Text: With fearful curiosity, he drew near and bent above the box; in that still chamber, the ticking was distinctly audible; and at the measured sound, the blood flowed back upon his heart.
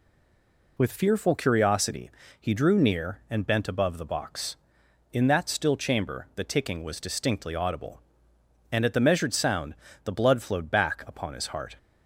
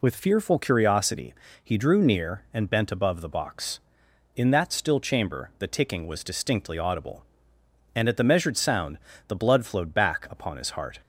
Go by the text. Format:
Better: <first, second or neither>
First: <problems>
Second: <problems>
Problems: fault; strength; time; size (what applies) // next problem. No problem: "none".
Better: second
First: stays silent before the first word; slight; until 0.7 s; 0.7 s long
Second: none